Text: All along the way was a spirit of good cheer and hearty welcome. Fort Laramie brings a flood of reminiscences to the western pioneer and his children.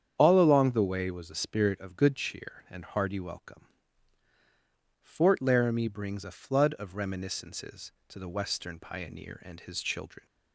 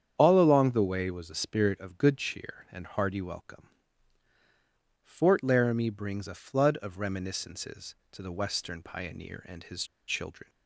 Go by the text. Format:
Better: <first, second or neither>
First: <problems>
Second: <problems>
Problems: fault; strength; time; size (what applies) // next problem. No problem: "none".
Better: first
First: starts louder than the rest; strong; until 1.1 s; 8.5 dB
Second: starts louder than the rest; strong; until 1.1 s; 8.5 dB // pauses between "his" and "children"; slight; at 9.8 s; 0.23 s long